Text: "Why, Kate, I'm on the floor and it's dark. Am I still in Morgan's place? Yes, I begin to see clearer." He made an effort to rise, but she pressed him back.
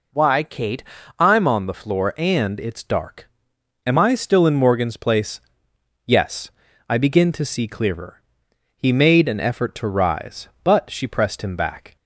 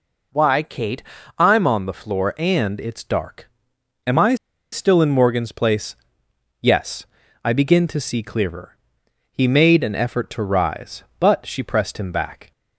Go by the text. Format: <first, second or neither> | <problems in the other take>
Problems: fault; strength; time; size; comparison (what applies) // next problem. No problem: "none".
first | pauses between "I" and "still"; slight; at 4.3 s; 0.35 s long